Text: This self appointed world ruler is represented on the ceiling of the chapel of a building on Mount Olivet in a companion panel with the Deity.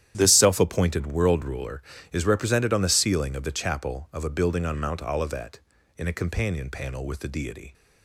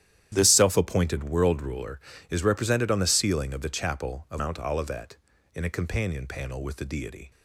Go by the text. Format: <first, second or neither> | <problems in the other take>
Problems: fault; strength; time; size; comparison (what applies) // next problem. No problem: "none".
first | starts louder than the rest; strong; until 1.3 s; 11 dB; strong in the first // skips "a building on"; at 4.3 s